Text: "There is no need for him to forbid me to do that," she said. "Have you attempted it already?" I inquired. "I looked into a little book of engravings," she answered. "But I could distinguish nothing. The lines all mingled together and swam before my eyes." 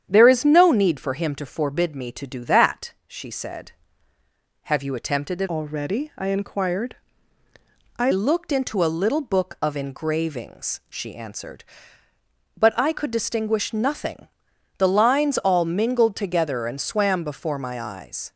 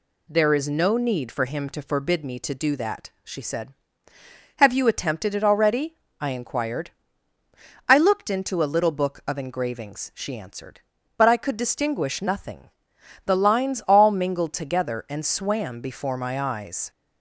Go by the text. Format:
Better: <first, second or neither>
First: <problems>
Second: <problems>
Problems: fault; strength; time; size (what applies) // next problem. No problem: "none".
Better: second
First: starts louder than the rest; strong; until 1.1 s; 9 dB // changes voice from "already" to "I"; from 5.4 to 8.1 s; 2.7 s long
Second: none